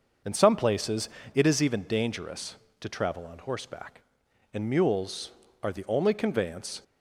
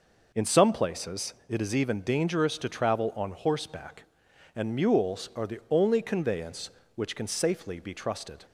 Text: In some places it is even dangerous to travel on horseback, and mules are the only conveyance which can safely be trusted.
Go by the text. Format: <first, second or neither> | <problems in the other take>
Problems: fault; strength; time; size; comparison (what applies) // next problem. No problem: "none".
second | starts louder than the rest; until 1.5 s; 6 dB // pauses between "places" and "it"; slight; at 1.0 s; 0.26 s long // stops before "which can safely be trusted"; at 6.8 s